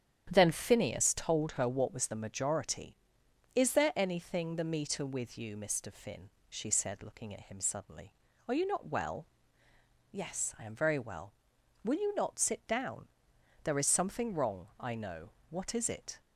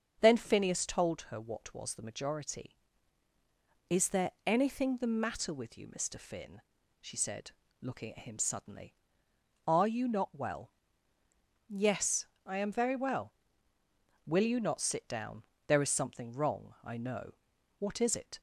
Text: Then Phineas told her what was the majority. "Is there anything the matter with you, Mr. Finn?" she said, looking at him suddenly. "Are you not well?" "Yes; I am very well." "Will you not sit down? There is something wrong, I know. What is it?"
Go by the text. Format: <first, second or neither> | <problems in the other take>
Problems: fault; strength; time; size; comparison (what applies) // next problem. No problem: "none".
second | starts louder than the rest; strong; until 1.3 s; 9.5 dB; also in the second // says "meter" for "matter"; at 4.7 s